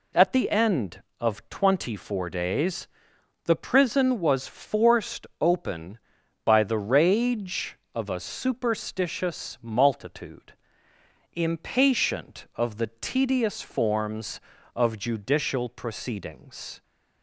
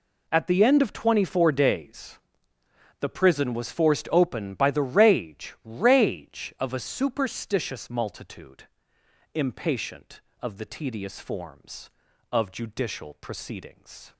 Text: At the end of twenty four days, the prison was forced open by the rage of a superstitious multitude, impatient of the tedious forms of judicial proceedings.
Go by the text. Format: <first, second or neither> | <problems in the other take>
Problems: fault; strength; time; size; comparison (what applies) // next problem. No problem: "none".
first | says "rage" twice; at 5.6 s